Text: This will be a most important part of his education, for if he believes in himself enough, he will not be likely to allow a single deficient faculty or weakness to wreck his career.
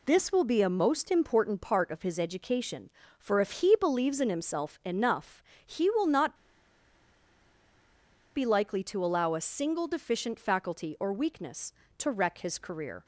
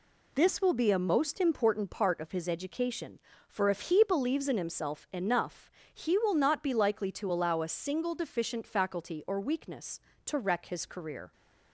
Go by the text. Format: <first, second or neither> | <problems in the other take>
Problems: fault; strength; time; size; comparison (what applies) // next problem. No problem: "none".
second | pauses between "not" and "be"; strong; at 6.3 s; 2.0 s long